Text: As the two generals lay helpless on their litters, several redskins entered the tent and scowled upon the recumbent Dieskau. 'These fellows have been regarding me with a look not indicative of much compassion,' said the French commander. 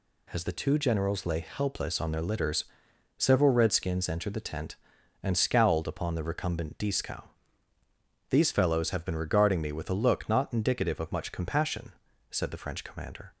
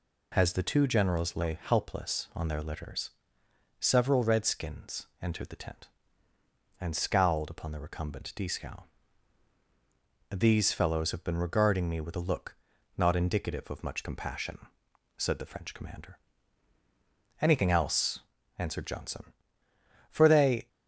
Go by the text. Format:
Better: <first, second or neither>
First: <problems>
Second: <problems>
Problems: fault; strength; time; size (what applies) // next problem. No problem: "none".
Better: first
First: none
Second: pauses between "redskins" and "entered"; slight; at 5.0 s; 0.16 s long // pauses between "look" and "not"; at 12.5 s; 0.42 s long // goes on to say "Anything else answered Johnson for they"; strong; from 17.4 s on; 3.2 s long